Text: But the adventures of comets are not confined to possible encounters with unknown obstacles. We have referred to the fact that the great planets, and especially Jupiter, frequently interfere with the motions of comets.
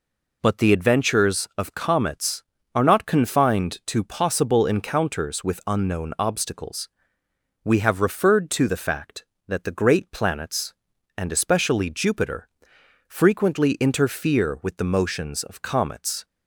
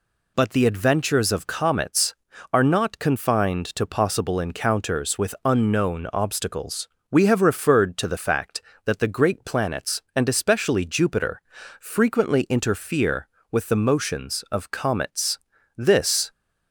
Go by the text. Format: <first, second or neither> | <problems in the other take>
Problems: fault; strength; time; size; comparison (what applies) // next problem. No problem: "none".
first | goes on to say "This"; from 15.7 s on; 0.54 s long